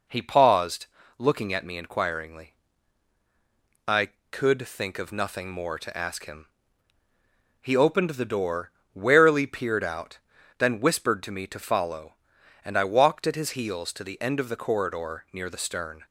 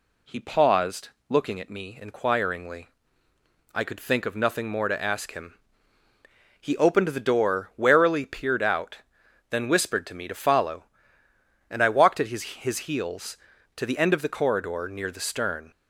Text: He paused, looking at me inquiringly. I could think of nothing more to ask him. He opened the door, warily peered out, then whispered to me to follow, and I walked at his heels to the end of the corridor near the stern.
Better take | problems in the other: first | says "his" twice; at 12.4 s

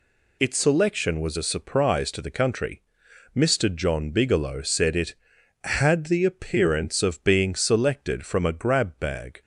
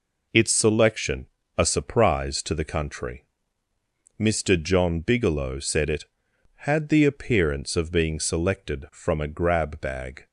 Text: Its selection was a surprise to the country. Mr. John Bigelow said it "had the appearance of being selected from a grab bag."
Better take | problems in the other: first | skips "was"; at 1.4 s

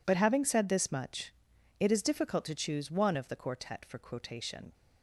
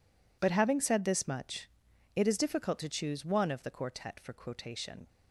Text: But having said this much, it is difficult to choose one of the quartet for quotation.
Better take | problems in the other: neither | none

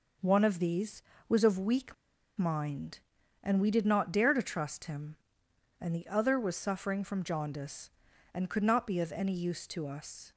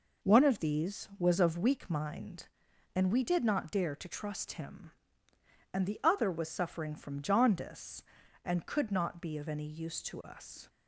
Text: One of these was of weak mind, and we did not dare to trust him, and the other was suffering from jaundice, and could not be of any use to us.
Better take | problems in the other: second | pauses between "weak" and "mind"; at 1.9 s; 0.42 s long

